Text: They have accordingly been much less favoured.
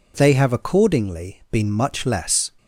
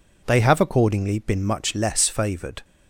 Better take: second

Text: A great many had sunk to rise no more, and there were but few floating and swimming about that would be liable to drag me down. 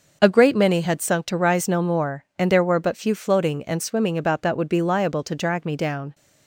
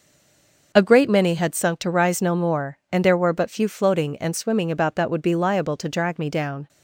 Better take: first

